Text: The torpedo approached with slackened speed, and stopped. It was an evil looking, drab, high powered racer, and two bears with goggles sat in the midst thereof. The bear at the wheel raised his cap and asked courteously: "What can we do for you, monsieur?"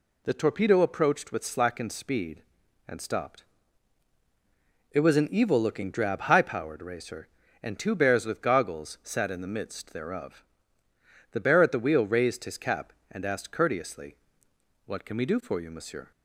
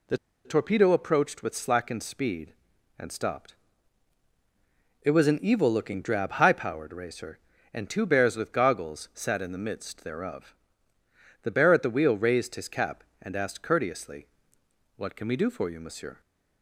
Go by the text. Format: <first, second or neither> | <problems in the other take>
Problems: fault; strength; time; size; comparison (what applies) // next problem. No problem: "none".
first | pauses between "The" and "torpedo"; slight; at 0.1 s; 0.27 s long